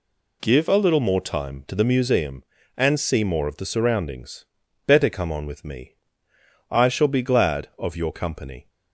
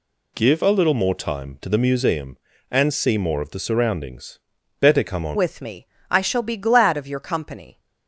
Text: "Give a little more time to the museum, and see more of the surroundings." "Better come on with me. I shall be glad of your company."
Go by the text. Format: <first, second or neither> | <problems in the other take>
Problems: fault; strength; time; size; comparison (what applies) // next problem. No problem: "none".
first | changes voice at "with"; from 5.3 s on; 2.4 s long